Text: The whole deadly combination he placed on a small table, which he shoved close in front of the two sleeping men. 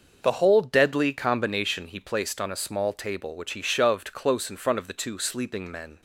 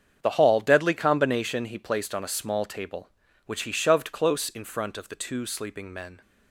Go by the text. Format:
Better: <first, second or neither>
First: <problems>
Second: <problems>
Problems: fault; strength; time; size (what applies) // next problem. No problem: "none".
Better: first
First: starts louder than the rest; until 1.2 s; 6 dB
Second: starts louder than the rest; strong; until 1.2 s; 7.5 dB // says "hall" for "whole"; at 0.3 s